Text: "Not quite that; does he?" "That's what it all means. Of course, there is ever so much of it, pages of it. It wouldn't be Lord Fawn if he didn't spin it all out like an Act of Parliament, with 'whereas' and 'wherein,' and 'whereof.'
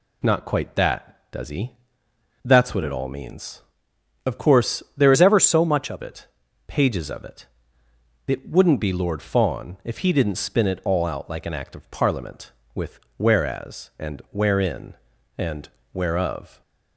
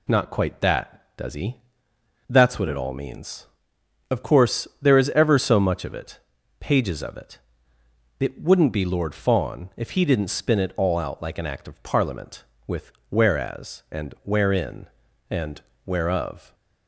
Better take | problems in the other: second | changes voice from "is" to "of"; from 5.1 to 6.0 s; 0.9 s long // pauses between "with" and "whereas"; slight; at 12.9 s; 0.18 s long; slight in the second // pauses between "and" and "whereof"; slight; at 15.6 s; 0.26 s long; slight in the second

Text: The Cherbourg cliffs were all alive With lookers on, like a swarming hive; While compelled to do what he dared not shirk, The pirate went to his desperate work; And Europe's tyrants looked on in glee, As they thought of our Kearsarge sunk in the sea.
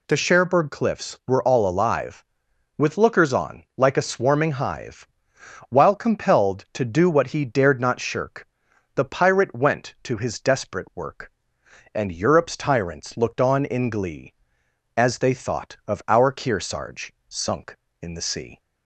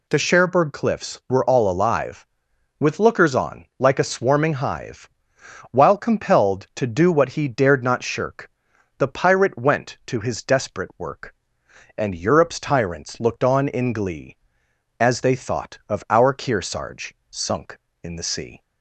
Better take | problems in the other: neither | pauses between "Kearsarge" and "sunk"; slight; the same in both

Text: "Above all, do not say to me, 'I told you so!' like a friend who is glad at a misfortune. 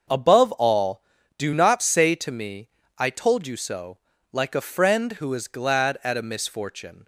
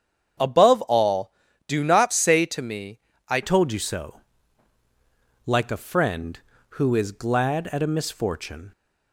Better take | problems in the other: first | starts louder than the rest; strong; until 1.7 s; 8 dB; also in the first // changes voice at "told"; from 3.4 s on; 5.3 s long

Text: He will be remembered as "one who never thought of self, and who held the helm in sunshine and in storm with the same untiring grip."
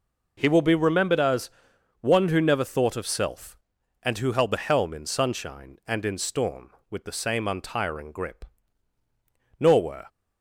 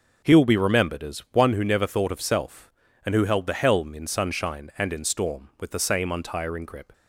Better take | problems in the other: second | pauses between "as" and "one"; noticeable; at 1.5 s; 0.50 s long // goes on to say "Nor were"; slight; from 9.5 s on; 0.48 s long

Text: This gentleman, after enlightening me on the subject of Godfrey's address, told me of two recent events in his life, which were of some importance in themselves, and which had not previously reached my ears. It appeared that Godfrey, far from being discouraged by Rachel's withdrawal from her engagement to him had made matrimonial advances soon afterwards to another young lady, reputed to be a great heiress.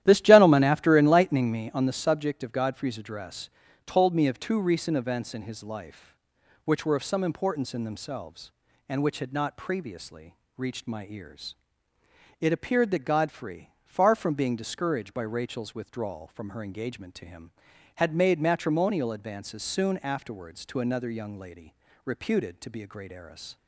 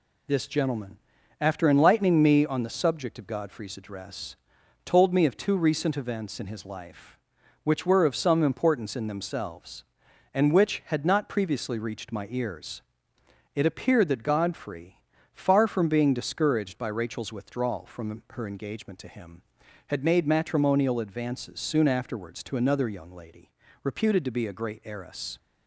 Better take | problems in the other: second | starts louder than the rest; strong; until 1.9 s; 12.5 dB // pauses between "previously" and "reached"; slight; at 10.3 s; 0.24 s long

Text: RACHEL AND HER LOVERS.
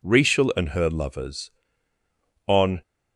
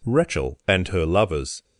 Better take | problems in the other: second | goes on to say "On"; slight; from 2.4 s on; 0.34 s long

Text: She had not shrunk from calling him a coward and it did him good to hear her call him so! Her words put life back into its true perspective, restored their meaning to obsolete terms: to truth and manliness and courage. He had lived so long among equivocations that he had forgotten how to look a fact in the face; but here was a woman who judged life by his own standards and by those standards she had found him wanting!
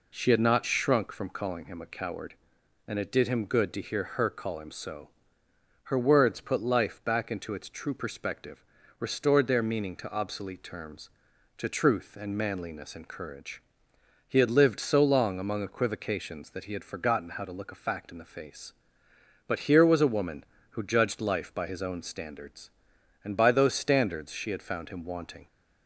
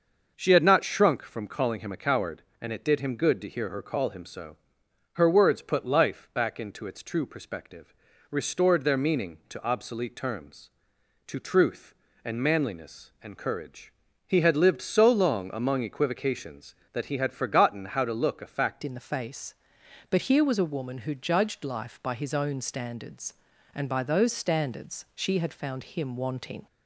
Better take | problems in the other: first | starts louder than the rest; until 1.3 s; 6 dB // changes voice at "in"; from 18.8 s on; 7.8 s long

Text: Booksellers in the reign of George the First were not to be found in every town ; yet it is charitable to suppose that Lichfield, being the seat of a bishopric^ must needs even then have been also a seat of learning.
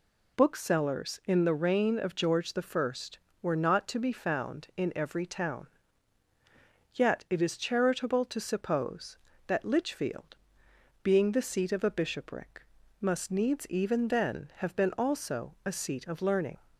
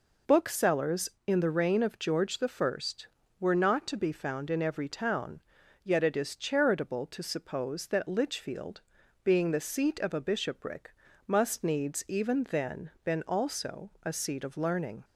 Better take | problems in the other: first | pauses between "bishopric" and "must"; slight; at 10.9 s; 0.36 s long; slight in the first // skips "have"; at 12.9 s

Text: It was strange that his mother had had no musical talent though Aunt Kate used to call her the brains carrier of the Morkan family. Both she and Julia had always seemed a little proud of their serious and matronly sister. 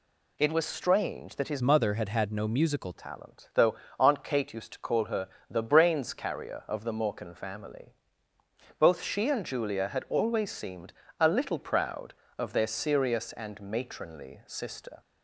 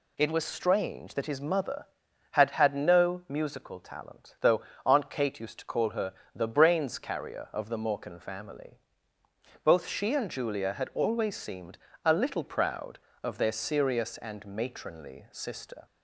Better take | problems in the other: second | changes voice from "mother" to "musical"; from 1.6 to 2.9 s; 1.3 s long // pauses between "though" and "Aunt"; slight; at 3.7 s; 0.24 s long; slight in the second // pauses between "her" and "the"; slight; at 5.2 s; 0.22 s long; slight in the second // pauses between "seemed" and "a"; slight; at 10.9 s; 0.26 s long; slight in the second

